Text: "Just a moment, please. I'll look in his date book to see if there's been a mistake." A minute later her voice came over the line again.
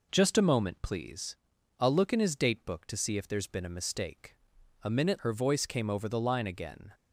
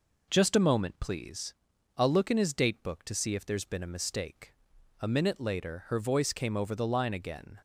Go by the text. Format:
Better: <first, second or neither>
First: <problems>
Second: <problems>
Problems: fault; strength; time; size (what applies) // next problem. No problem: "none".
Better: second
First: skips "later"; at 5.2 s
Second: none